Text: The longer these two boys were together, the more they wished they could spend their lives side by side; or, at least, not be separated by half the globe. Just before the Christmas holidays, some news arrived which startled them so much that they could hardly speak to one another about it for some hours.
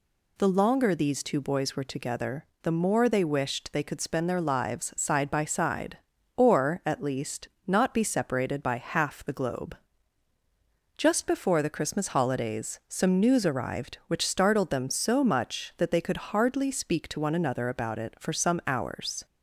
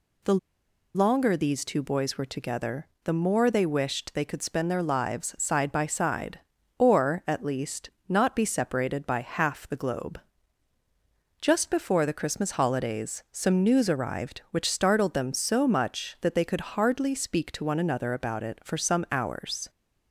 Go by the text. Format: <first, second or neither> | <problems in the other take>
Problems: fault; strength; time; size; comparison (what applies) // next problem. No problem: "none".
first | pauses between "The" and "longer"; noticeable; at 0.3 s; 0.60 s long